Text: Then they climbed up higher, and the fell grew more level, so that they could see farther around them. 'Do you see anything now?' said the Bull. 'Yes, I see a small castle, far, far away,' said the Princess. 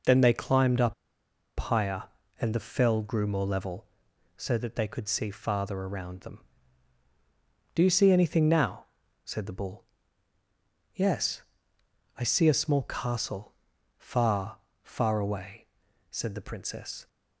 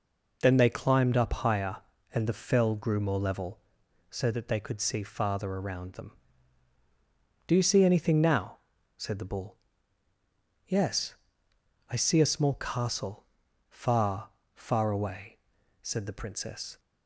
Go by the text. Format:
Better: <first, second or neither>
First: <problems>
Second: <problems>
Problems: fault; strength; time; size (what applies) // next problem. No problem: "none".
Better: second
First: pauses between "up" and "higher"; noticeable; at 0.9 s; 0.65 s long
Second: none